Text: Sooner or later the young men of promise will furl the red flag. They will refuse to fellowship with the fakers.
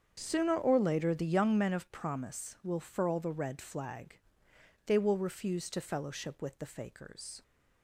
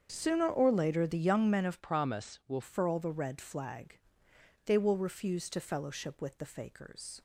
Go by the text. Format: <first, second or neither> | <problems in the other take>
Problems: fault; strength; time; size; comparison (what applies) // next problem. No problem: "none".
first | starts louder than the rest; strong; until 1.1 s; 7.5 dB; strong in the first // changes voice from "promise" to "will"; from 1.8 to 2.6 s; 0.8 s long